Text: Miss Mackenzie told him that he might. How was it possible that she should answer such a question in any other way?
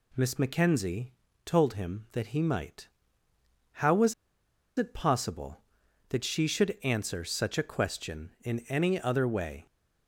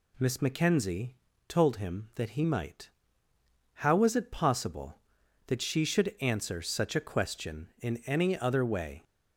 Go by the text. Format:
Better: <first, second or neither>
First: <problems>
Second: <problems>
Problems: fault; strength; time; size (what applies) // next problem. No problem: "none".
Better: second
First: pauses between "Mackenzie" and "told"; slight; at 1.1 s; 0.34 s long // pauses between "was" and "it"; noticeable; at 4.1 s; 0.64 s long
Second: pauses between "Mackenzie" and "told"; slight; at 1.1 s; 0.34 s long